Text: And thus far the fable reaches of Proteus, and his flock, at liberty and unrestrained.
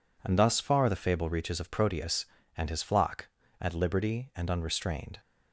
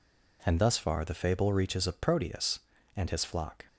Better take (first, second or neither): first